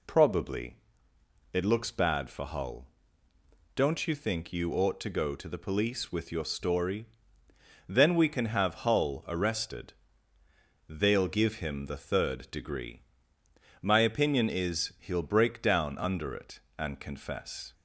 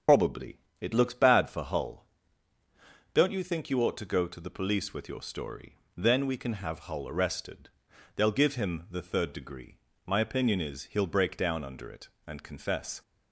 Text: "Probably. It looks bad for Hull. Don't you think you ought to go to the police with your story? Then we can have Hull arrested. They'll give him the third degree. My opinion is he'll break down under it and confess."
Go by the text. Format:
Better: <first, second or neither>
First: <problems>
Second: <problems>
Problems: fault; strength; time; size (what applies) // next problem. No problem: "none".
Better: first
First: none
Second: loses the start of "Probably"; at 0.0 s; 50 ms // starts louder than the rest; strong; until 1.3 s; 8 dB